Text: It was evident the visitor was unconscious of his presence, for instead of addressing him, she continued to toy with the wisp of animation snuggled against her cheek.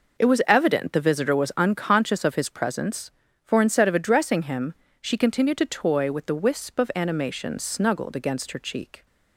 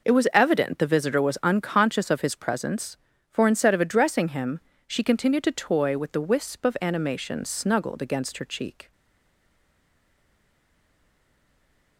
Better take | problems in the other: first | stays silent after the last word; strong; from 8.9 s on; 3.0 s long

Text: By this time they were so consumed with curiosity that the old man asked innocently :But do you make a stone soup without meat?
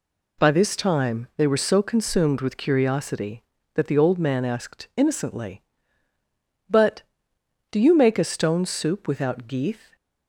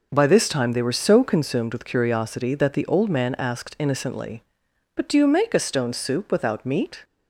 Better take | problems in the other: second | says "geeth" for "meat"; at 9.4 s

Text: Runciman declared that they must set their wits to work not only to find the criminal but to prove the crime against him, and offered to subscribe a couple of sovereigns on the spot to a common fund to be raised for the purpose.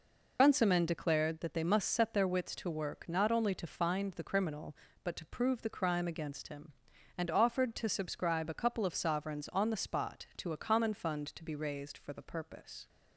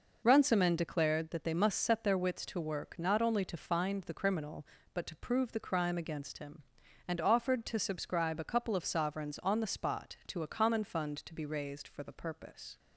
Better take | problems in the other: second | loses the start of "Runciman"; at 0.3 s; 55 ms

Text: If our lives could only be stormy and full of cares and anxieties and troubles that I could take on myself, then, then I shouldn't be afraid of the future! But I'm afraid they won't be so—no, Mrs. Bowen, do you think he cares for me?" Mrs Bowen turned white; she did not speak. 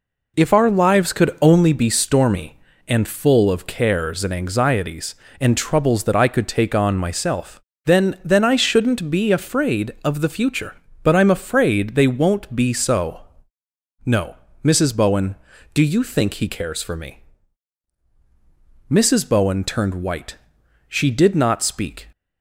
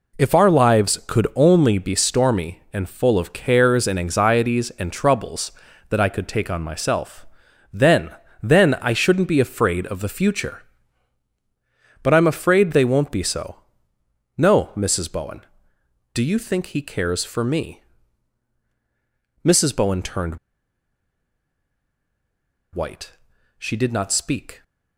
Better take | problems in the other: first | pauses between "turned" and "white"; strong; at 20.3 s; 2.3 s long

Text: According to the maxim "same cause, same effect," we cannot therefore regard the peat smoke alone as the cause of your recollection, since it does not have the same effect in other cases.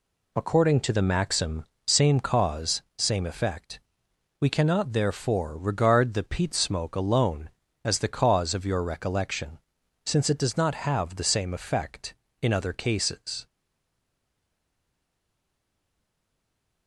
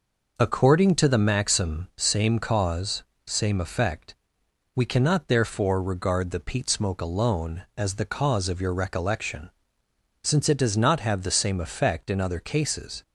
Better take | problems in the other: second | pauses between "maxim" and "same"; slight; at 1.6 s; 0.20 s long // stays silent after the last word; strong; from 13.4 s on; 3.4 s long

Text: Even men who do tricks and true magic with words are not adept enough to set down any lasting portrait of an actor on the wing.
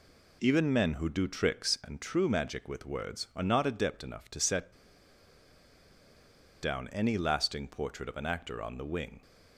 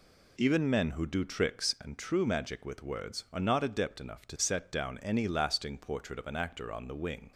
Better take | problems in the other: second | pauses between "set" and "down"; strong; at 4.7 s; 1.8 s long

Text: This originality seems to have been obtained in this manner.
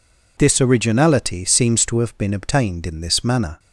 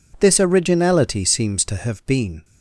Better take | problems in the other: first | stops before "obtained in this manner"; at 2.4 s

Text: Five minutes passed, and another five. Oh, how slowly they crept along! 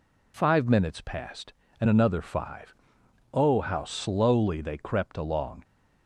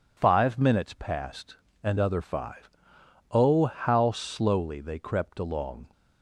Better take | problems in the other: first | says "other" for "another"; at 1.9 s

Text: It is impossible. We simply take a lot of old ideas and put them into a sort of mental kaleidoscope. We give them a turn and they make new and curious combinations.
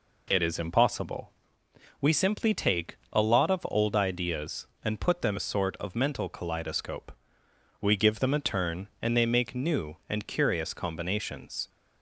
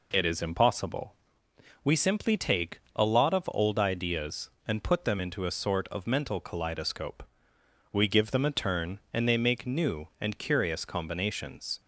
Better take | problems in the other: second | skips "into"; at 5.3 s

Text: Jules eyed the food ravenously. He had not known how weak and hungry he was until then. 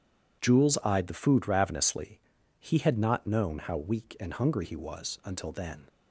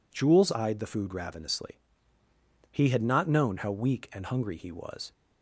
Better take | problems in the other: first | stops before "until then"; at 5.1 s

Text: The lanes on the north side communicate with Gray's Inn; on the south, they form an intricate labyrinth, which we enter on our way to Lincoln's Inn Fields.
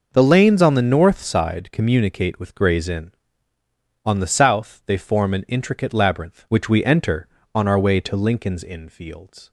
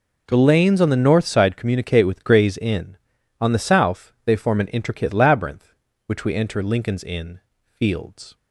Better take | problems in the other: first | skips "on our way to"; at 6.6 s // pauses between "Inn" and "Fields"; slight; at 7.4 s; 0.26 s long

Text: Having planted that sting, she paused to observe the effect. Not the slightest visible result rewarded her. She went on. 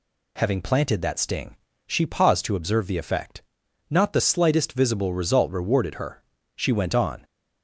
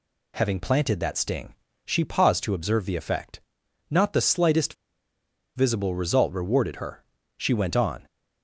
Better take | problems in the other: first | pauses between "slightest" and "visible"; noticeable; at 4.7 s; 0.82 s long

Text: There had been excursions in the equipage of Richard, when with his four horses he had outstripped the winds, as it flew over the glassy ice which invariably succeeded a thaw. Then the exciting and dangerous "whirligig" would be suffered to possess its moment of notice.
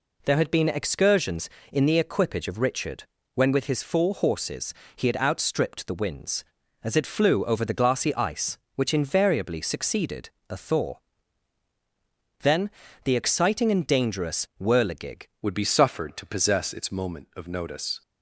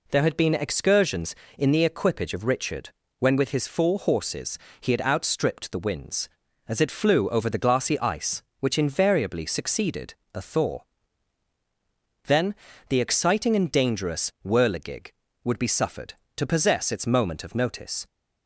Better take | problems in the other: second | pauses between "horses" and "he"; slight; at 4.7 s; 0.22 s long; slight in the second // pauses between "succeeded" and "a"; slight; at 10.2 s; 0.20 s long; slight in the second // pauses between "Then" and "the"; slight; at 12.6 s; 0.34 s long; slight in the second // changes voice at "would"; from 15.4 s on; 2.6 s long

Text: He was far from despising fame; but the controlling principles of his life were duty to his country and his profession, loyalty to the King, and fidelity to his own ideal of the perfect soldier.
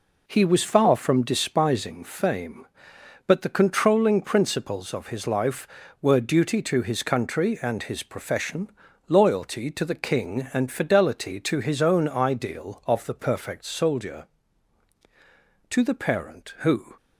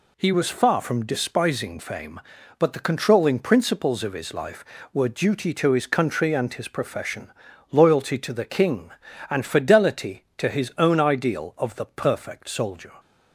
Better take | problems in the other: second | goes on to say "To the parent who"; noticeable; from 15.6 s on; 1.2 s long

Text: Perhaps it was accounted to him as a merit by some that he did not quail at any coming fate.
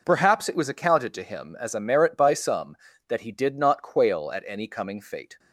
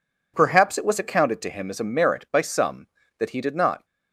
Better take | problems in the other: first | stops before "quail at any coming fate"; at 3.8 s

